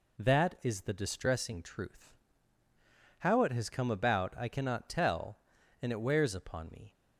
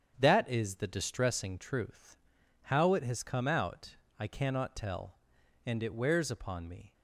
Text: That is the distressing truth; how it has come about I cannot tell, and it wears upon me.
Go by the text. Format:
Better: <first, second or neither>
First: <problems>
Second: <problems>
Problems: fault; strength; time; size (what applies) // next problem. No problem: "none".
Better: first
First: none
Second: starts louder than the rest; strong; until 1.1 s; 8 dB // says "out" for "about"; at 3.4 s